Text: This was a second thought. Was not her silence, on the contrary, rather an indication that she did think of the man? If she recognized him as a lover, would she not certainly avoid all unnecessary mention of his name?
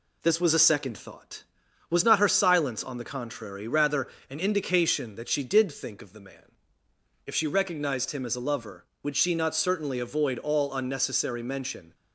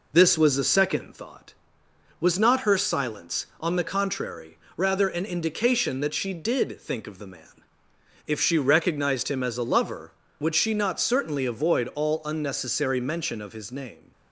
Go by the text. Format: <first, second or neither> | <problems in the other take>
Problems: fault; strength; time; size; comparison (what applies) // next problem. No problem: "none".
second | pauses between "rather" and "an"; slight; at 4.0 s; 0.22 s long // stops before "of his name"; at 11.9 s